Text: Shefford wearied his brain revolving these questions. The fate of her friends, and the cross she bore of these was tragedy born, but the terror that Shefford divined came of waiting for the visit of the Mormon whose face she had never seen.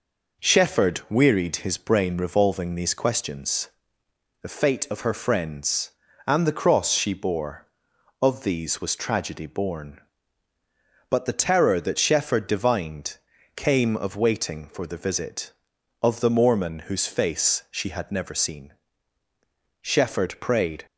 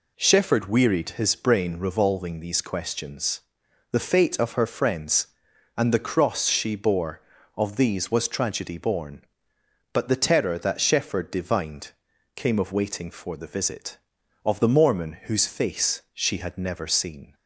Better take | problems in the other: second | pauses between "divined" and "came"; at 13.1 s; 0.38 s long; noticeable in the second // goes on to say "Shefford prayed"; noticeable; from 19.8 s on; 1.0 s long

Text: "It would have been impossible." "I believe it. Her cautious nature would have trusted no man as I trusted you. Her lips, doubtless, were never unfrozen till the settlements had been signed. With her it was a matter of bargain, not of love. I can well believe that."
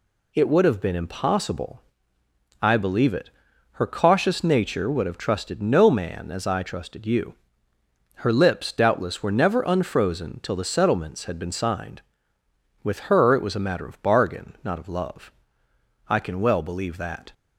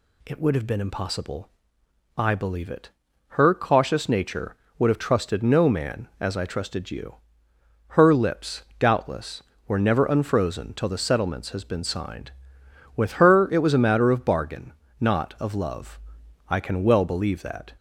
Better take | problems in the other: first | says "has" for "had"; at 11.4 s

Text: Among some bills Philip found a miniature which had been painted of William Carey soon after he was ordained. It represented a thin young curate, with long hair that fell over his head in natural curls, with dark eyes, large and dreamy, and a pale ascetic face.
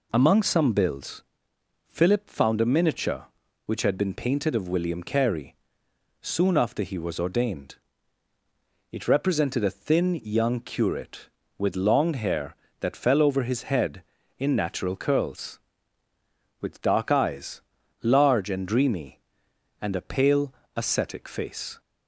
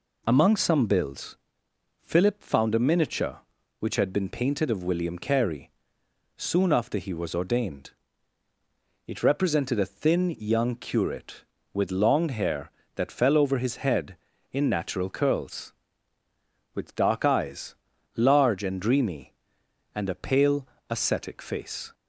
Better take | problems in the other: neither | pauses between "bills" and "Philip"; noticeable; the same in both // pauses between "Carey" and "soon"; noticeable; the same in both // pauses between "pale" and "ascetic"; slight; the same in both

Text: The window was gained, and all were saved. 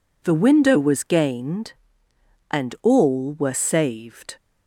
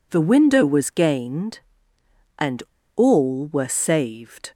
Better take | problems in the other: first | pauses between "and" and "all"; slight; at 2.6 s; 0.33 s long

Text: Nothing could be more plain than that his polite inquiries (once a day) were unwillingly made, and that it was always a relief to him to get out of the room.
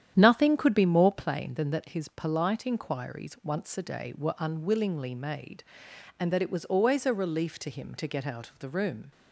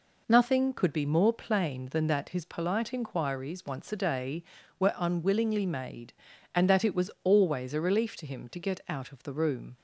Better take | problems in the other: second | starts louder than the rest; strong; until 1.4 s; 9.5 dB

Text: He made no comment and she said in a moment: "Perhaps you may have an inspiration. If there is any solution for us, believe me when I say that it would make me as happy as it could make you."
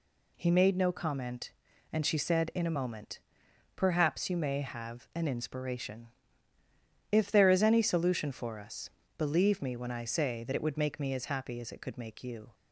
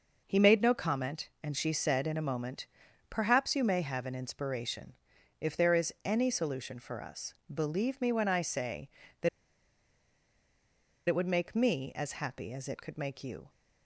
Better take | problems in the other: first | pauses between "that" and "it"; strong; at 9.2 s; 1.8 s long

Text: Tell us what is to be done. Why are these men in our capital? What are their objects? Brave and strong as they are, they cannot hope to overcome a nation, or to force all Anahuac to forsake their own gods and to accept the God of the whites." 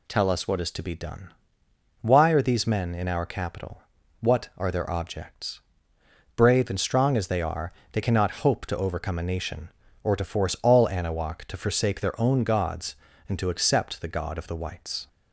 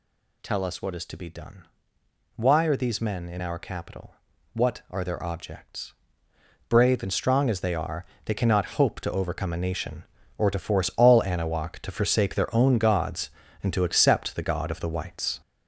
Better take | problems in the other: first | gets louder; noticeable; throughout; 6 dB

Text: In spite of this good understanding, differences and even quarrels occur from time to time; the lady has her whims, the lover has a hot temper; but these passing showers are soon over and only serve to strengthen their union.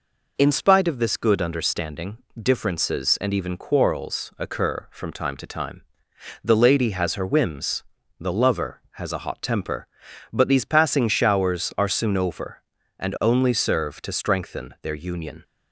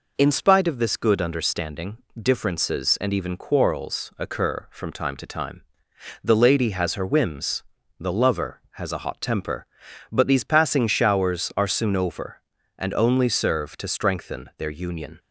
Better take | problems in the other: neither | none

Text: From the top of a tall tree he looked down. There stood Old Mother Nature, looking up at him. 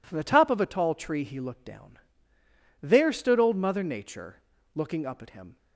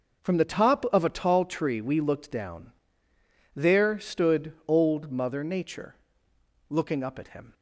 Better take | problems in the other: first | says "we" for "he"; at 1.7 s

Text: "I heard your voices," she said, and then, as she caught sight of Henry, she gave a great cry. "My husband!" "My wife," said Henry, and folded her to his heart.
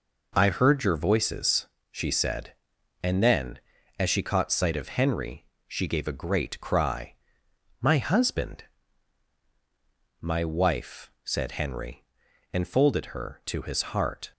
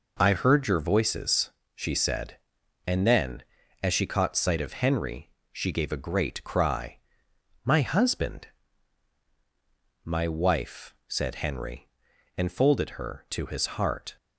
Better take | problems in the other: neither | none

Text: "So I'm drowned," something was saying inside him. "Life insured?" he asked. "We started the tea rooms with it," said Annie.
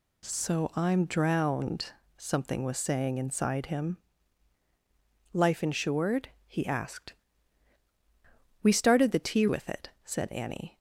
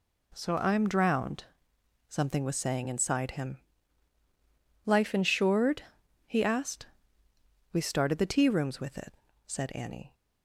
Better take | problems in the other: second | skips "rooms"; at 9.4 s

